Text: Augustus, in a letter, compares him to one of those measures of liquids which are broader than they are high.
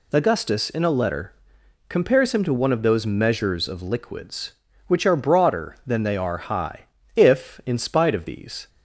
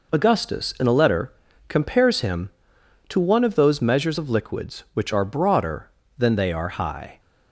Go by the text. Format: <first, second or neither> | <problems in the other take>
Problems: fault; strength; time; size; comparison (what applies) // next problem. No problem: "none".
second | goes on to say "If in spite of these"; from 7.1 s on; 1.5 s long